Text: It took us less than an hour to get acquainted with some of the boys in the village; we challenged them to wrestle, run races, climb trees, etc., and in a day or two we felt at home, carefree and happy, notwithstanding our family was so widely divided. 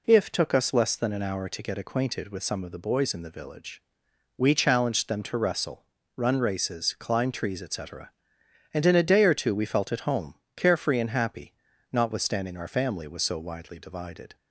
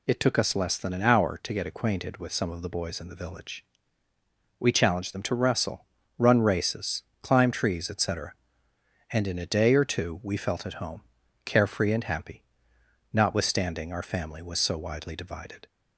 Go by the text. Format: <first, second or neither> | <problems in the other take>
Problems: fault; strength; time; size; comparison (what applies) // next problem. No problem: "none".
second | says "If" for "It"; at 0.0 s